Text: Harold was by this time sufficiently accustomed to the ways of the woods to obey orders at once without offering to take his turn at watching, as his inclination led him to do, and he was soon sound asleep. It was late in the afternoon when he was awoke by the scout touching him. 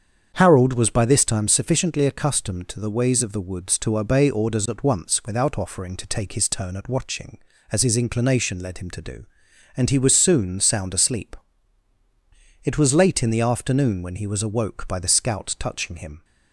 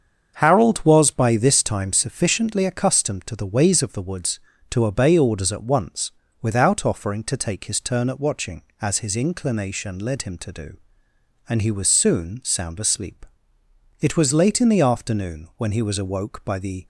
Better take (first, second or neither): first